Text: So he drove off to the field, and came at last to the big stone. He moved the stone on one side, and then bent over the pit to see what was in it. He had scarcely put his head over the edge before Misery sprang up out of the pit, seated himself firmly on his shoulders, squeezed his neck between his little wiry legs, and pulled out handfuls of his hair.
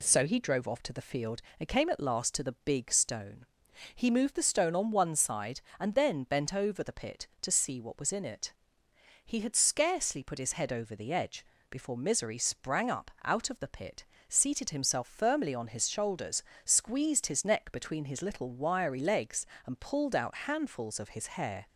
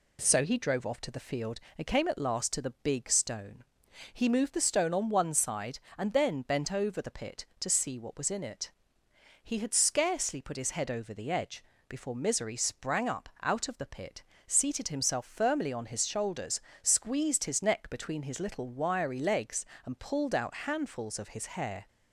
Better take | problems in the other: neither | pauses between "edge" and "before"; slight; the same in both

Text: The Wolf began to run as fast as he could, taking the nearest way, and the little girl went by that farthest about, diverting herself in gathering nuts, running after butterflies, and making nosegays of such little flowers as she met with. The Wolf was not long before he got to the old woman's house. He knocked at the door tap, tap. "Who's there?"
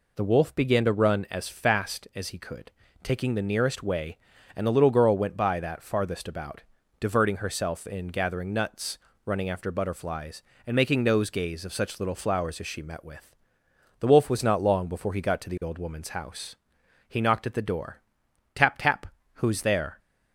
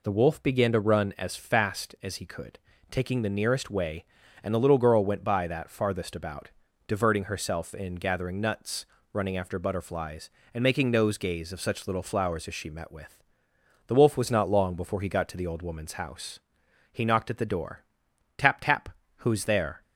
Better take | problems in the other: neither | pauses between "door" and "tap"; noticeable; the same in both

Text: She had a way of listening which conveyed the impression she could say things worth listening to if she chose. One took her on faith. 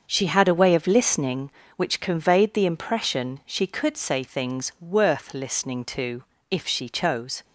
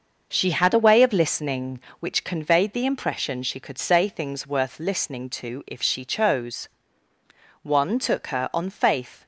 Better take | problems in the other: second | starts louder than the rest; until 1.1 s; 7 dB; noticeable in the second // pauses between "to" and "if"; slight; at 6.2 s; 0.26 s long // stops before "One took her on faith"; at 7.4 s

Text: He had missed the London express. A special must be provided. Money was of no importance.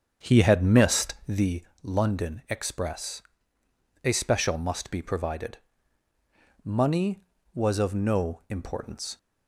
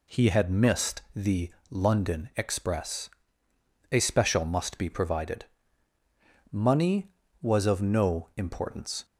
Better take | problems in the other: second | starts louder than the rest; until 1.6 s; 7 dB // pauses between "the" and "London"; slight; at 1.6 s; 0.18 s long; slight in the second

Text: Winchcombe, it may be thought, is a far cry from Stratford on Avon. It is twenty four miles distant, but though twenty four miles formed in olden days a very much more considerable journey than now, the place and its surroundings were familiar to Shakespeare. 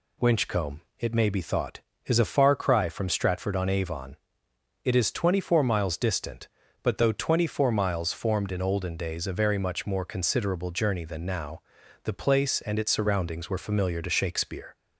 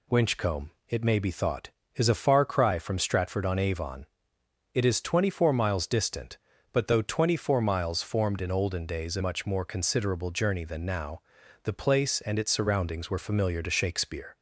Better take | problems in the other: first | skips "very"; at 9.2 s

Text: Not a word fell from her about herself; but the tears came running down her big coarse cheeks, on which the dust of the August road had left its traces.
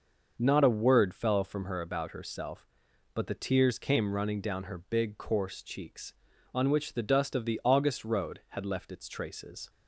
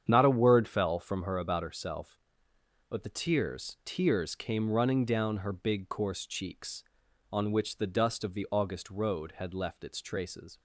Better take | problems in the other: first | starts louder than the rest; strong; until 1.1 s; 8.5 dB // says "tears" twice; at 3.8 s

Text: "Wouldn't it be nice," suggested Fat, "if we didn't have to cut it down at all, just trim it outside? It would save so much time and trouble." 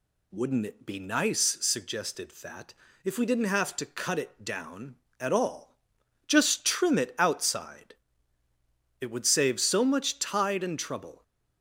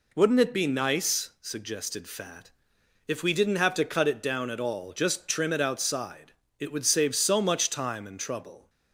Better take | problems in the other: second | says "tide" for "time"; at 10.1 s

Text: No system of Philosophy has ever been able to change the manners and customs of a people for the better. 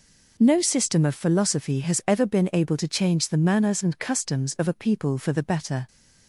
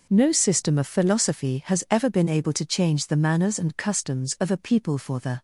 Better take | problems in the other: first | stops before "better"; at 5.3 s

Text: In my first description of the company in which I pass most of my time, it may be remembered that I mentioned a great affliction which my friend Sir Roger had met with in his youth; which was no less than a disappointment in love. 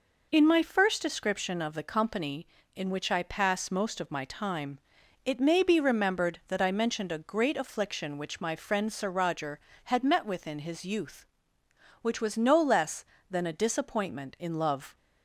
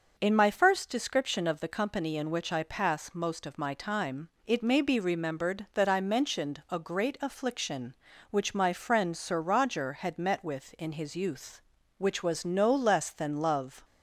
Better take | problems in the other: first | skips "a disappointment in"; at 13.3 s

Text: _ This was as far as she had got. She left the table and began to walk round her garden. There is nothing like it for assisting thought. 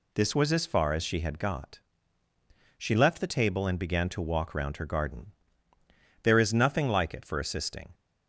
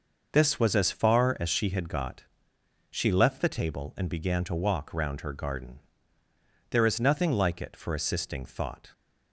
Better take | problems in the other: second | stops before "thought"; at 7.9 s

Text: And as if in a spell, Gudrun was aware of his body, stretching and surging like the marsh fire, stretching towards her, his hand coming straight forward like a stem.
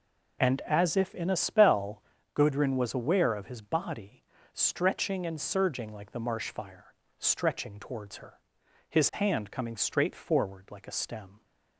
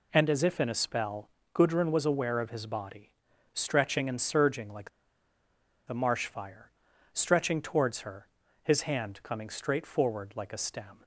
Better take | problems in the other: first | pauses between "like" and "the"; noticeable; at 4.8 s; 0.97 s long

